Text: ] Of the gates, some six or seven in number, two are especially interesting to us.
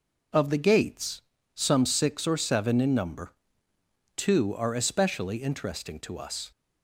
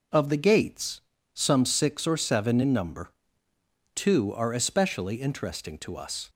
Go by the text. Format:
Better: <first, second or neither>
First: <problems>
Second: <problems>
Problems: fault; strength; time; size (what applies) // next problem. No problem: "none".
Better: neither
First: none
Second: none